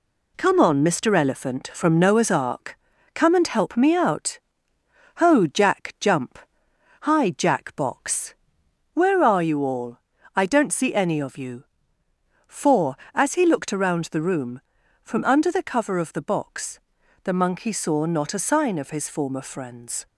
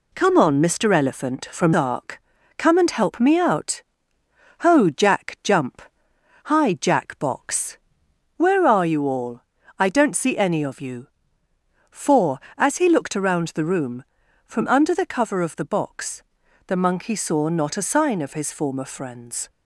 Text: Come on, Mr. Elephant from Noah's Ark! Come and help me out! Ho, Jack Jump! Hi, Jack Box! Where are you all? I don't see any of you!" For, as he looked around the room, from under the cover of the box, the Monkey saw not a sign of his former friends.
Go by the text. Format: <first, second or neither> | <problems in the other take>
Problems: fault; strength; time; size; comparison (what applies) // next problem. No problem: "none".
first | skips "Noah's"; at 1.7 s